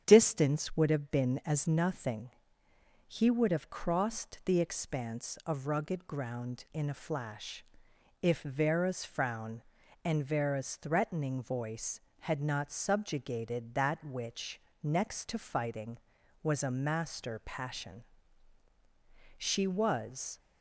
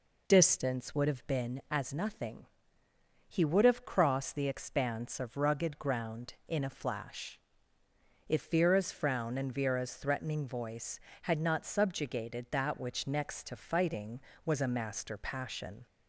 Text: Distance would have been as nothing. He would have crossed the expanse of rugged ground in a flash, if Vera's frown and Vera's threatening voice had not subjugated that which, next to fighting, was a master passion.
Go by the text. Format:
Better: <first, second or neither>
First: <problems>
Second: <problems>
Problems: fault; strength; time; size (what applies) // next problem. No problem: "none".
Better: second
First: starts louder than the rest; strong; until 1.0 s; 8.5 dB // goes on to say "She was"; noticeable; from 19.3 s on; 1.0 s long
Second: none